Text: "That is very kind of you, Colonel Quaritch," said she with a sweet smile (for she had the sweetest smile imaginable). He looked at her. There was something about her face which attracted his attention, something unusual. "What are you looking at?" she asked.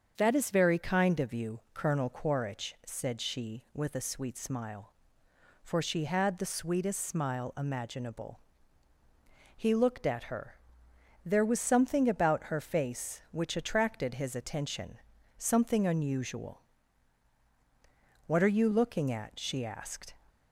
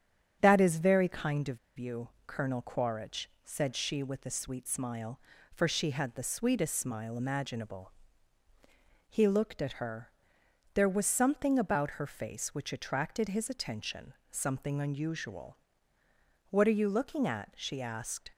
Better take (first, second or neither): first